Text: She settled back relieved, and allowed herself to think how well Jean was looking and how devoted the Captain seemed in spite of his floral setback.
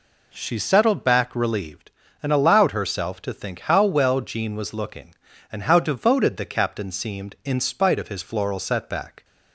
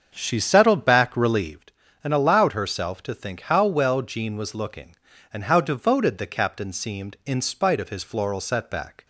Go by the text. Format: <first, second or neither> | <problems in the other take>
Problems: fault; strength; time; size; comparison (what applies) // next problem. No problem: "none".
first | starts louder than the rest; until 1.6 s; 7 dB